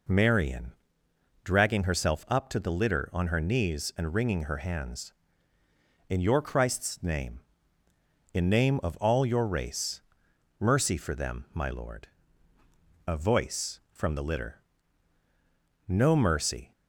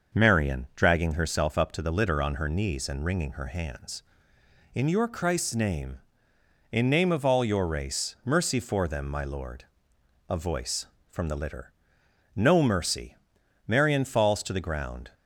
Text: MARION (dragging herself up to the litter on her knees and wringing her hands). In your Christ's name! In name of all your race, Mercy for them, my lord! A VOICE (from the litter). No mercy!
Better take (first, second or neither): first